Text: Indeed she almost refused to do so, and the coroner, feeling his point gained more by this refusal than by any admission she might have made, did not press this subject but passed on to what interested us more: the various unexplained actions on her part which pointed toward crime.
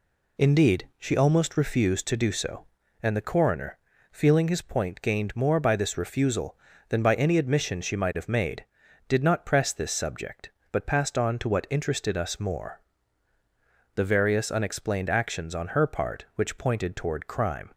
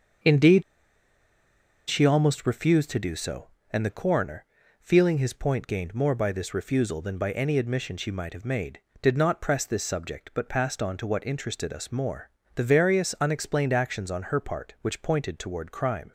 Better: first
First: none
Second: starts louder than the rest; until 2.4 s; 7 dB // pauses between "Indeed" and "she"; strong; at 0.6 s; 1.2 s long

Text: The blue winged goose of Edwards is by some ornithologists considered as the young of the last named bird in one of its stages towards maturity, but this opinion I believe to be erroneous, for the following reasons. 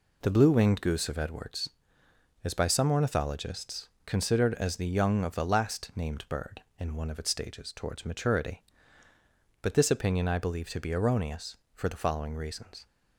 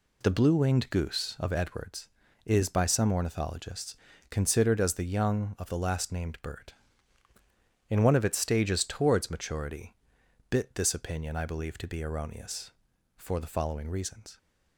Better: first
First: pauses between "ornithologists" and "considered"; slight; at 3.8 s; 0.18 s long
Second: pauses between "ornithologists" and "considered"; slight; at 3.9 s; 0.34 s long // says "bit" for "but"; at 10.4 s

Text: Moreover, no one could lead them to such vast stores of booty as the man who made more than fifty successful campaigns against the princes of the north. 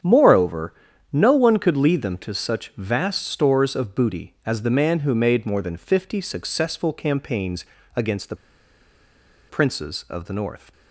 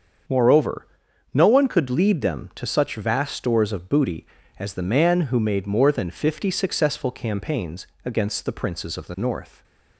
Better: second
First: starts louder than the rest; strong; until 1.4 s; 8.5 dB // pauses between "campaigns" and "against"; slight; at 7.6 s; 0.32 s long // pauses between "the" and "princes"; at 8.3 s; 1.1 s long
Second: starts louder than the rest; until 1.7 s; 7 dB // pauses between "campaigns" and "against"; slight; at 7.8 s; 0.18 s long

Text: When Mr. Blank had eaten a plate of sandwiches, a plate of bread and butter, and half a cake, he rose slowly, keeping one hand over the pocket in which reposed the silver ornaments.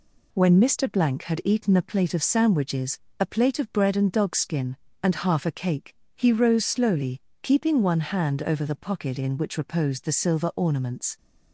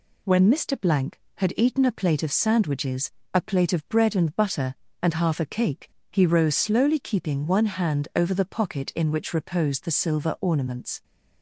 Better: second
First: says "dogskin" for "butter"; at 4.1 s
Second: none

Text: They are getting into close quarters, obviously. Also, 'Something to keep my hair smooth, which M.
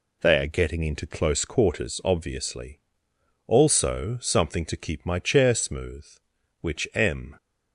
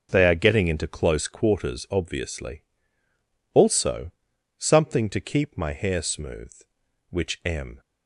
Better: second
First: says "chair" for "hair"; at 5.1 s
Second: none

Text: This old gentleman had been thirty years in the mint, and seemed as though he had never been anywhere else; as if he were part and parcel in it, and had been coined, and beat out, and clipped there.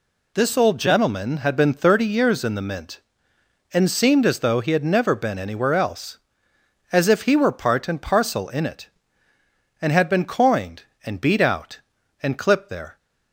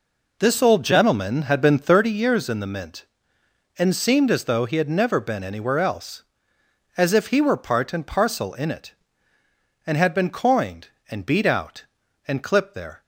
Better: first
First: none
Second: starts louder than the rest; noticeable; until 2.1 s; 4 dB

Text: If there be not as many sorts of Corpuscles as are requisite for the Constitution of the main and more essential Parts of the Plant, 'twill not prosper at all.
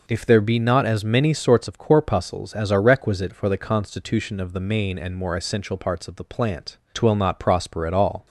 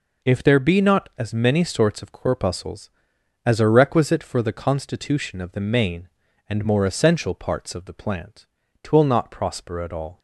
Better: neither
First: none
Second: none

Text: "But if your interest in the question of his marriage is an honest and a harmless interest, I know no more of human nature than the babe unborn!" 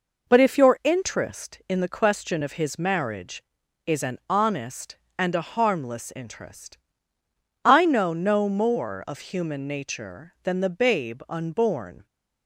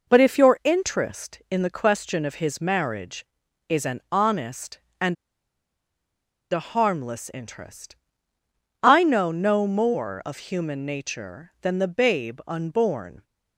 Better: first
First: none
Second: pauses between "and" and "a"; strong; at 5.1 s; 1.3 s long

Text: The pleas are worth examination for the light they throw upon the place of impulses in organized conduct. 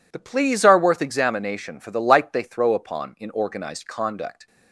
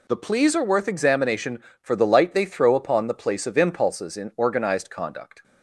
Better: second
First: skips "the place of impulses"; at 3.1 s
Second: none

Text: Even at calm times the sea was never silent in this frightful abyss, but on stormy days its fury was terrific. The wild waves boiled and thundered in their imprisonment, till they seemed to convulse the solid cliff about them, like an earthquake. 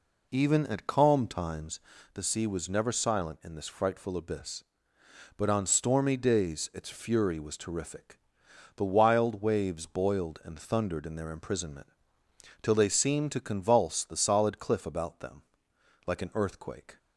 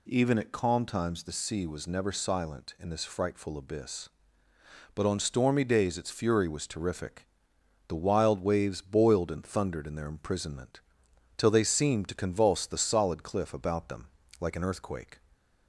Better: second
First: starts louder than the rest; until 2.1 s; 3.5 dB // pauses between "times" and "the"; slight; at 1.7 s; 0.34 s long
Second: none

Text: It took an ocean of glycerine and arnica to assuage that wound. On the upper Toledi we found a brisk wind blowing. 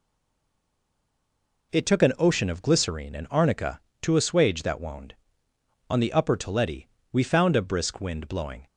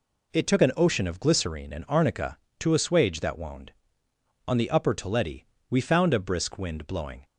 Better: second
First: stays silent before the first word; noticeable; until 1.7 s; 1.7 s long // pauses between "Toledi" and "we"; slight; at 6.8 s; 0.24 s long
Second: pauses between "Toledi" and "we"; slight; at 5.4 s; 0.24 s long

